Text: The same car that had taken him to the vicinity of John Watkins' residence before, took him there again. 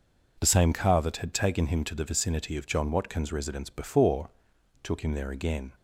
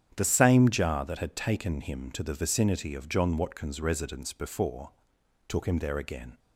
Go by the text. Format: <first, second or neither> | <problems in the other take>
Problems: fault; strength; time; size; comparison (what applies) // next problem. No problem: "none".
first | starts louder than the rest; strong; until 1.1 s; 9.5 dB // says "jar" for "car"; at 0.6 s